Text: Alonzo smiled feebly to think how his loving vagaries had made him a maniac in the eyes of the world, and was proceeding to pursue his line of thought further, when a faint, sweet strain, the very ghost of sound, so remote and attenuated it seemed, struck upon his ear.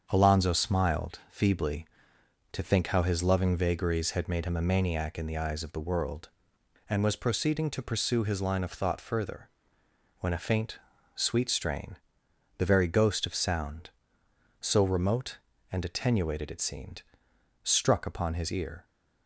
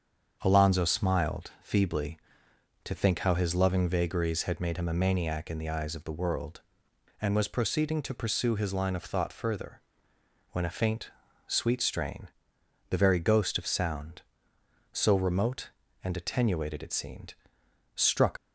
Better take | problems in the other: first | starts louder than the rest; strong; until 1.4 s; 7 dB; strong in the first // stops before "upon his ear"; at 18.3 s

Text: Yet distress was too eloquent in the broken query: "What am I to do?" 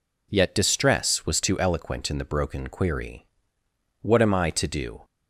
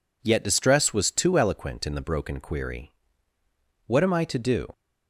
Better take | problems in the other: neither | none

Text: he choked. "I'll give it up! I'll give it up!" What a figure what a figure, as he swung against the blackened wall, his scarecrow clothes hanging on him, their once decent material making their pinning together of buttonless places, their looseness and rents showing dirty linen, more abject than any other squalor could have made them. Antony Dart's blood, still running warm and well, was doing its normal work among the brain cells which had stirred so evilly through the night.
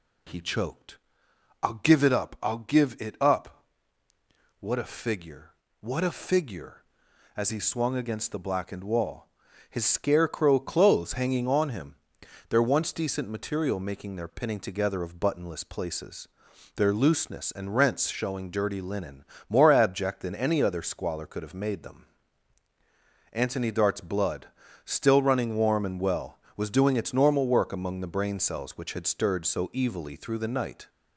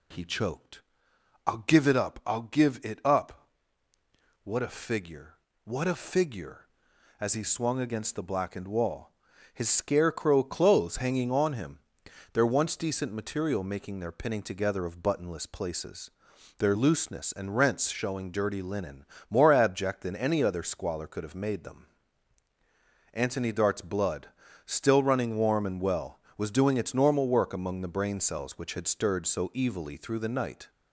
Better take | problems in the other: neither | pauses between "figure" and "what"; slight; the same in both

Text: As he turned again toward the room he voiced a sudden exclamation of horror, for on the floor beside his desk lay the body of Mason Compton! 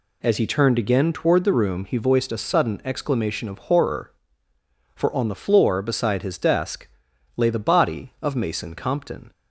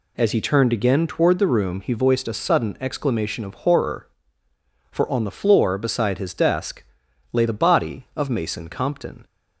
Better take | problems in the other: neither | pauses between "desk" and "lay"; noticeable; the same in both

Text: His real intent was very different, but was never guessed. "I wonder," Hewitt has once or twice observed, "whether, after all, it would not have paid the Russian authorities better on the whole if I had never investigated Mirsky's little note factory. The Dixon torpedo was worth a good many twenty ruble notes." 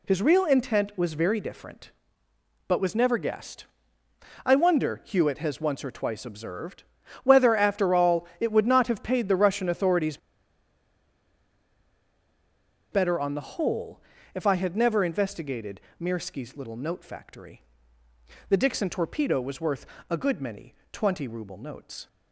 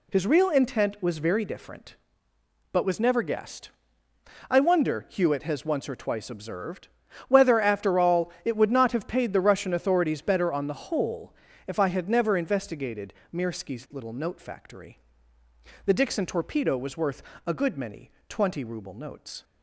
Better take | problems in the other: second | pauses between "authorities" and "better"; strong; at 10.1 s; 2.7 s long // pauses between "whole" and "if"; slight; at 14.0 s; 0.34 s long; slight in the second // pauses between "investigated" and "Mirsky's"; slight; at 15.8 s; 0.18 s long; slight in the second // pauses between "worth" and "a"; slight; at 19.8 s; 0.24 s long; slight in the second // pauses between "many" and "twenty"; slight; at 20.7 s; 0.16 s long; slight in the second

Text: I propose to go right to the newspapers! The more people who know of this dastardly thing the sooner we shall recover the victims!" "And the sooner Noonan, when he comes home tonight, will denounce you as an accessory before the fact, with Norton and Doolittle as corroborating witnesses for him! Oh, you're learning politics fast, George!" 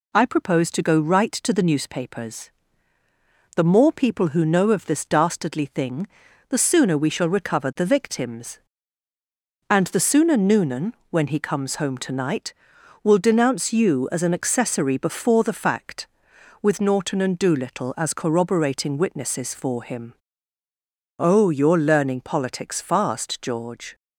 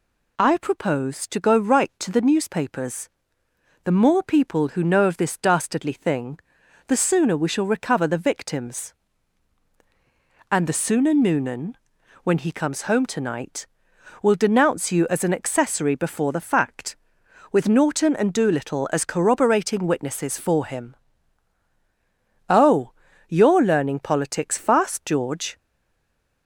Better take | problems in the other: first | pauses between "thing" and "the"; noticeable; at 6.3 s; 0.48 s long; also in the first // stays silent after the last word; slight; from 25.5 s on; 0.9 s long

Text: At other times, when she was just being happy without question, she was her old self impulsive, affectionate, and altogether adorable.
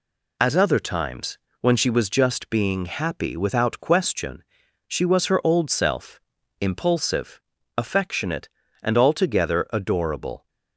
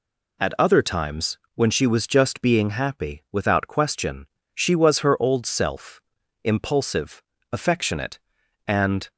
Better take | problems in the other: first | pauses between "self" and "impulsive"; at 6.0 s; 0.44 s long; also in the first // stops before "altogether adorable"; at 9.1 s

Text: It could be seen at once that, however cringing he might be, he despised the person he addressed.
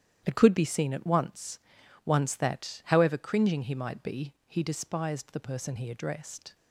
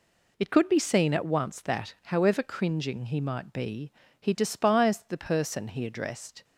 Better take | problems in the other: second | starts louder than the rest; strong; until 1.2 s; 10.5 dB // says "once" twice; at 2.0 s

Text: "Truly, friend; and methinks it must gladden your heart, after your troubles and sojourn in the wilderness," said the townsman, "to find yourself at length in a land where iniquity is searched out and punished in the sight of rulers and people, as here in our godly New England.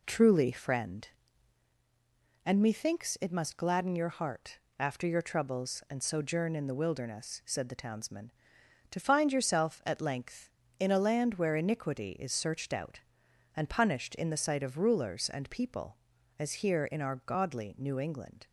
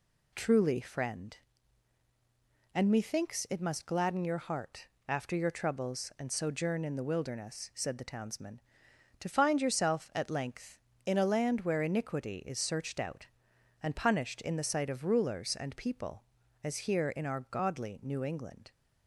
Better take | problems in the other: second | starts louder than the rest; slight; until 1.7 s; 3 dB

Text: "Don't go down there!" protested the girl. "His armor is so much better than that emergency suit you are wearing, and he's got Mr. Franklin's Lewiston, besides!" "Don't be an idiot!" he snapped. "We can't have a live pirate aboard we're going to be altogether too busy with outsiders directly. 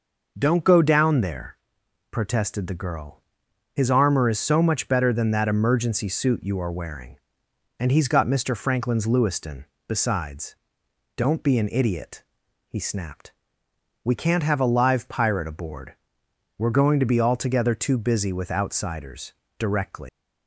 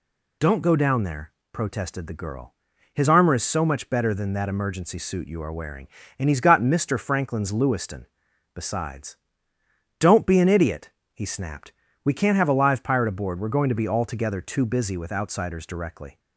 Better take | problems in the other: second | pauses between "aboard" and "we're"; noticeable; at 15.9 s; 0.62 s long // pauses between "outsiders" and "directly"; slight; at 19.3 s; 0.26 s long // leaves "directly" unfinished; at 20.0 s; 140 ms

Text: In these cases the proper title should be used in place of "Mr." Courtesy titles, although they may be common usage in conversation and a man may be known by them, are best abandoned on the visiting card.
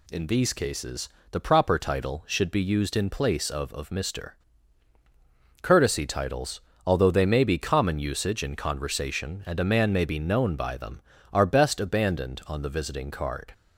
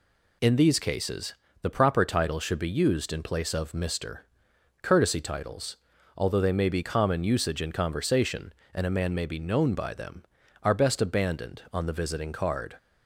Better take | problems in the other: second | pauses between "cases" and "the"; slight; at 1.0 s; 0.24 s long; slight in the second // says "of" twice; at 3.7 s

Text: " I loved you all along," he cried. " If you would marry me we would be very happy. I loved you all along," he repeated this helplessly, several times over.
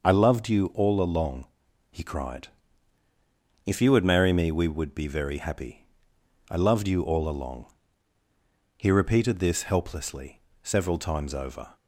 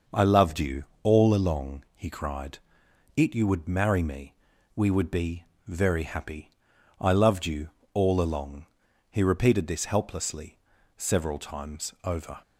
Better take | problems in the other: first | pauses between "you" and "all"; slight; at 0.8 s; 0.18 s long // says "It" for "If"; at 3.1 s // pauses between "me" and "we"; at 4.3 s; 0.42 s long // pauses between "be" and "very"; slight; at 5.4 s; 0.24 s long // pauses between "you" and "all"; slight; at 7.7 s; 0.22 s long

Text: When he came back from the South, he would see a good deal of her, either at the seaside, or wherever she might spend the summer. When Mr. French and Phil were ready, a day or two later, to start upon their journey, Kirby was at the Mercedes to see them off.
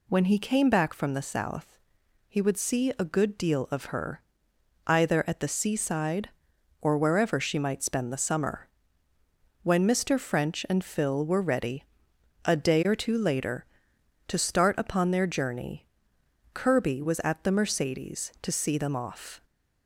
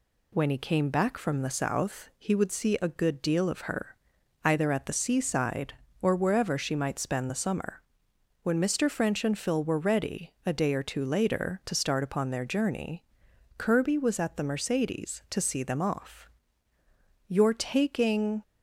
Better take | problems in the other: first | goes on to say "You're taking"; noticeable; from 17.2 s on; 1.1 s long

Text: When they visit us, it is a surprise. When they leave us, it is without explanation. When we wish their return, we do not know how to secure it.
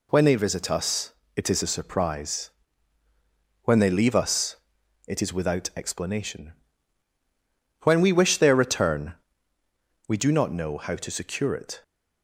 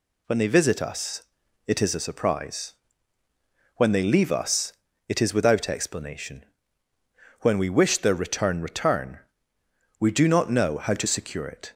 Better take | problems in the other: first | says "return" twice; at 8.6 s

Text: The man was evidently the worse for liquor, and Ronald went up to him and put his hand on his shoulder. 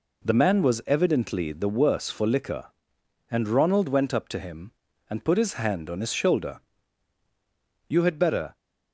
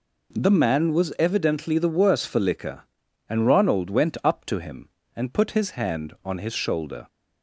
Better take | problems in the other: second | goes on to say "You had better"; noticeable; from 7.8 s on; 0.66 s long

